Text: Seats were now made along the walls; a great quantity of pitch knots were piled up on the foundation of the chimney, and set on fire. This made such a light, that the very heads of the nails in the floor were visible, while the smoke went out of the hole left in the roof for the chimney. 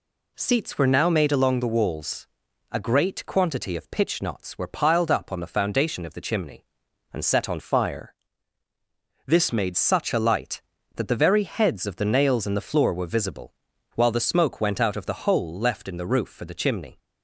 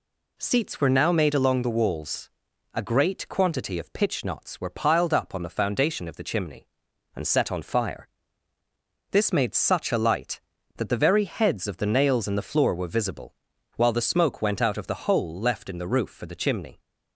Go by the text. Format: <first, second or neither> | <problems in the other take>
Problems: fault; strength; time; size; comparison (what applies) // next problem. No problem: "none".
second | changes voice from "fire" to "made"; from 7.6 to 9.7 s; 2.1 s long